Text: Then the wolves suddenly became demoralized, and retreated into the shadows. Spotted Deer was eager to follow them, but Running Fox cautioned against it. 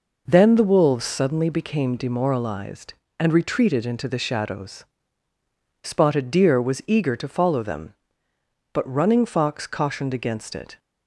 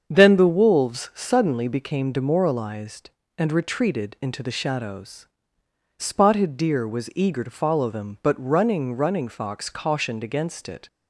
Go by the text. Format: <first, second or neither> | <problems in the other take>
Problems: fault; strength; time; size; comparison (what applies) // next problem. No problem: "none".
first | starts louder than the rest; until 1.0 s; 7 dB // says "Running" twice; at 8.9 s